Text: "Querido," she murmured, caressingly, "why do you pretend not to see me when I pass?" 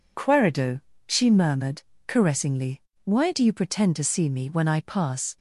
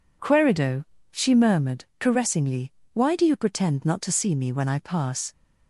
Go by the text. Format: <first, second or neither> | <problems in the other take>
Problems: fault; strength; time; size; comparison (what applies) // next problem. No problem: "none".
second | skips "not"; at 3.9 s